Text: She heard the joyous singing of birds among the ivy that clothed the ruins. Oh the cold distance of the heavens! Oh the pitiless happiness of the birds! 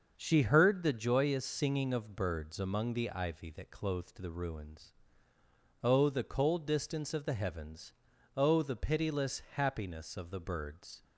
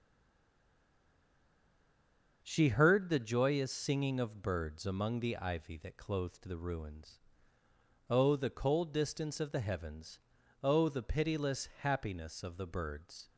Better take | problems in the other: first | stays silent before the first word; until 2.4 s; 2.4 s long // starts louder than the rest; until 3.4 s; 6 dB; also in the first

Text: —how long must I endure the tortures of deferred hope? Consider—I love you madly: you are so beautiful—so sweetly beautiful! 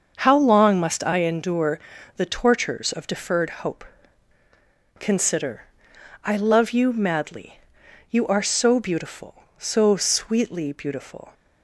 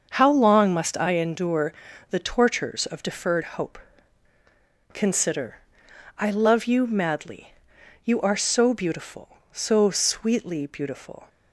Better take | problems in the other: neither | starts louder than the rest; the same in both // pauses between "endure" and "the"; slight; the same in both

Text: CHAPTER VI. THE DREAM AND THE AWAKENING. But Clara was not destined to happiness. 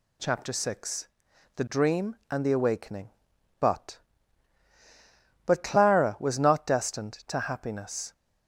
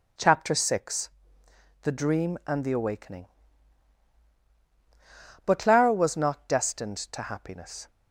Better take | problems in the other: second | says "But" twice; at 5.4 s

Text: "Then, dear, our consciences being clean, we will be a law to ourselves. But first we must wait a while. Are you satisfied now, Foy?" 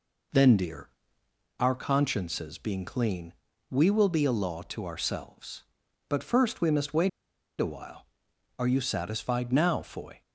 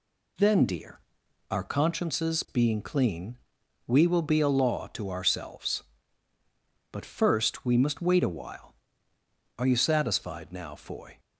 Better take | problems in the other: second | pauses between "wait" and "a"; noticeable; at 7.0 s; 0.51 s long

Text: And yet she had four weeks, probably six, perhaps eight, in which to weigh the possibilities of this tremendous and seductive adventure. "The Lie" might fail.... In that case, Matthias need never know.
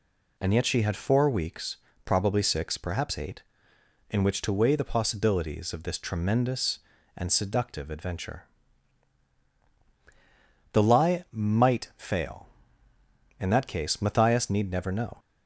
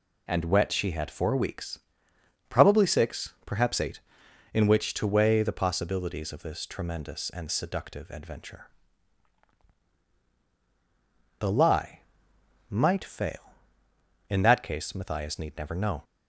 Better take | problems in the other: first | says "wet" for "yet"; at 0.4 s // pauses between "Lie" and "might"; noticeable; at 12.0 s; 0.68 s long

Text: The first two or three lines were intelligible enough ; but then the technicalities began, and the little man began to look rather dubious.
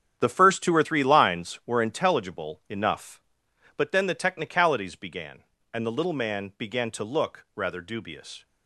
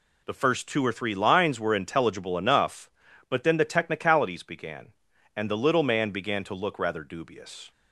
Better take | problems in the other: second | gets quieter; strong; throughout; 11.5 dB

